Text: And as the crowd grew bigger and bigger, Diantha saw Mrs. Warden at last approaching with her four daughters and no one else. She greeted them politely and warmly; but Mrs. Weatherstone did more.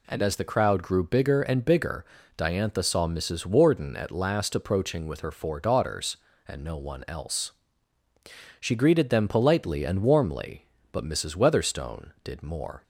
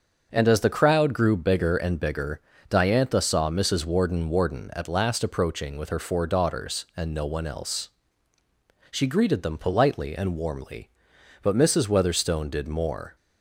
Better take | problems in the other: first | starts louder than the rest; until 1.3 s; 6.5 dB // says "Warden" twice; at 4.2 s

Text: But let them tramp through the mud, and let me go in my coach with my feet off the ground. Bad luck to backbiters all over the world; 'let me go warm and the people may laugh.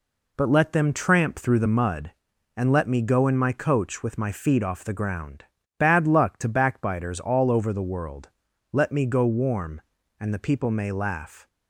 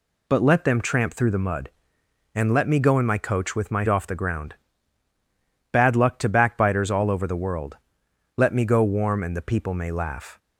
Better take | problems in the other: first | skips "feet"; at 3.8 s

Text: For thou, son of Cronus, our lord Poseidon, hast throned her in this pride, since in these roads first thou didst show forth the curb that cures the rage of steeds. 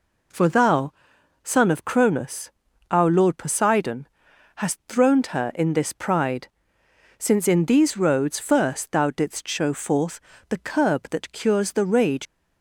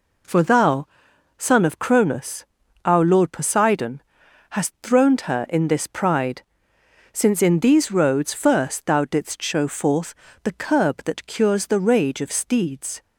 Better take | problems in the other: second | pauses between "forth" and "the"; slight; at 10.1 s; 0.30 s long; slight in the second // stops before "of steeds"; at 12.2 s

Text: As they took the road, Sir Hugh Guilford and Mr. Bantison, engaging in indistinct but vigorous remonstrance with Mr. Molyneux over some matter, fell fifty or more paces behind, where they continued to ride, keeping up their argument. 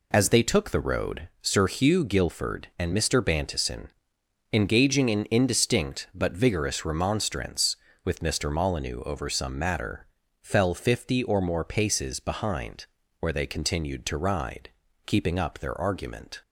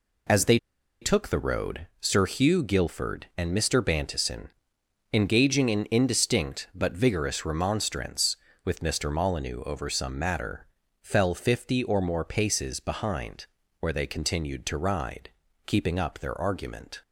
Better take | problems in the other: first | pauses between "they" and "took"; at 0.5 s; 0.43 s long

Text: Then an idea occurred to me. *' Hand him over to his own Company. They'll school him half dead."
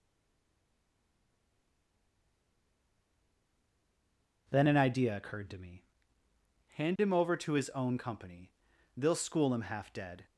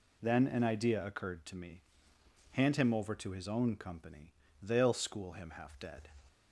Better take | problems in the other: second | stays silent before the first word; strong; until 4.4 s; 4.4 s long

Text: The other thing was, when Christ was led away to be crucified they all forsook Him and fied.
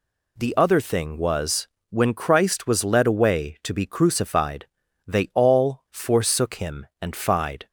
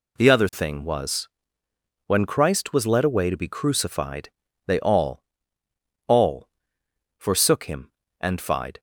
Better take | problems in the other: first | pauses between "crucified" and "they"; slight; at 4.2 s; 0.36 s long; also in the first // says "all" twice; at 6.0 s

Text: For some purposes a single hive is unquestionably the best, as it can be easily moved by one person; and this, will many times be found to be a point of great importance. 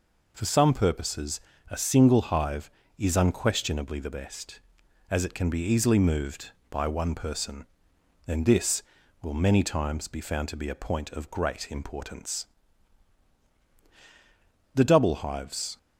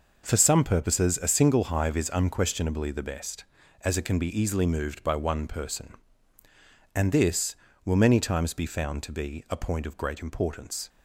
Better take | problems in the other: second | pauses between "purposes" and "a"; slight; at 1.3 s; 0.30 s long // goes on to say "The double hives"; noticeable; from 14.7 s on; 1.0 s long

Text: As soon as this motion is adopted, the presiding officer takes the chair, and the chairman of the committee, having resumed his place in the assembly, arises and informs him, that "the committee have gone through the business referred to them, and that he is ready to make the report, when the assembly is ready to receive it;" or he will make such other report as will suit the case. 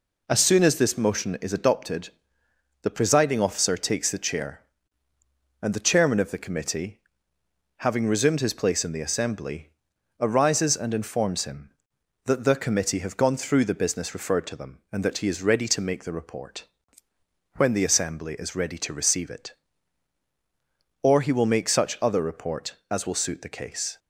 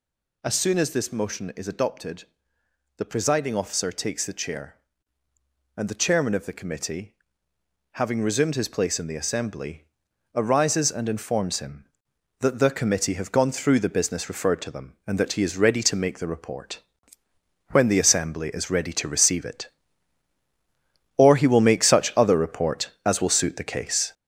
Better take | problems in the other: first | gets louder; noticeable; throughout; 6 dB

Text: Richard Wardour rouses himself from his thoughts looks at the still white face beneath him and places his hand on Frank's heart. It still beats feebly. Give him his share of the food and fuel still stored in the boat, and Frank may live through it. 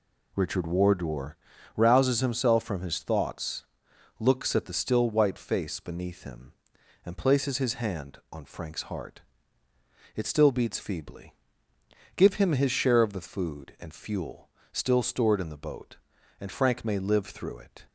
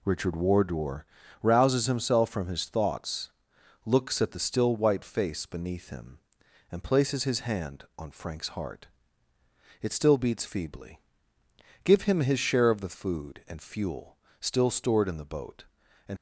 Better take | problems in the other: first | pauses between "Wardour" and "rouses"; slight; at 1.0 s; 0.36 s long; also in the first // pauses between "thoughts" and "looks"; noticeable; at 3.2 s; 0.54 s long; noticeable in the first // pauses between "fuel" and "still"; slight; at 14.1 s; 0.24 s long; slight in the first // stops before "Frank may live through it"; at 16.1 s

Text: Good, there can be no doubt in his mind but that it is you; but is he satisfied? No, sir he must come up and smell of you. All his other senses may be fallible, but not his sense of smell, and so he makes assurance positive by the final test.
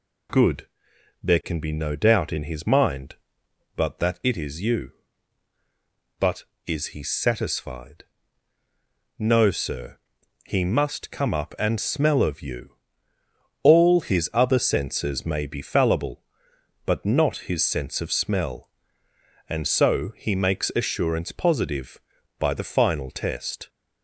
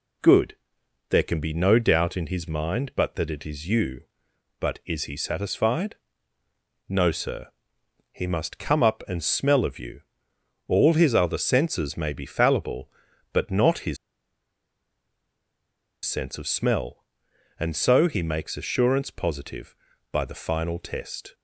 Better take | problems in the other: first | pauses between "sir" and "he"; noticeable; at 7.4 s; 0.64 s long; noticeable in the first // pauses between "his" and "sense"; strong; at 13.9 s; 2.0 s long

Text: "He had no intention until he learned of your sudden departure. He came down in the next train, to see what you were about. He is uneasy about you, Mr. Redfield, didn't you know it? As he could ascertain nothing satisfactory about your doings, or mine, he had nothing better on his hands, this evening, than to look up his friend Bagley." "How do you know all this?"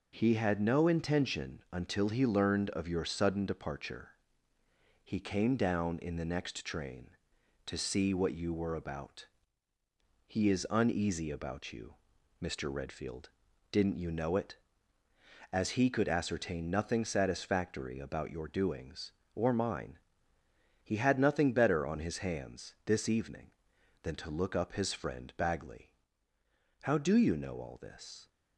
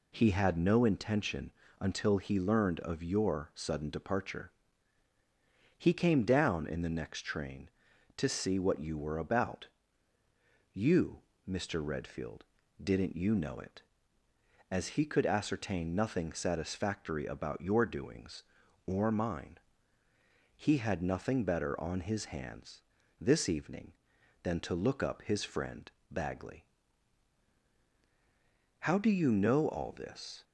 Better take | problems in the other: first | pauses between "intention" and "until"; slight; at 1.5 s; 0.28 s long // skips "He is uneasy about"; at 10.1 s // pauses between "friend" and "Bagley"; slight; at 25.8 s; 0.22 s long

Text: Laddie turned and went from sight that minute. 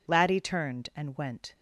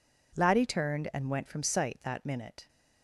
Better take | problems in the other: second | stops before "from sight that minute"; at 1.5 s

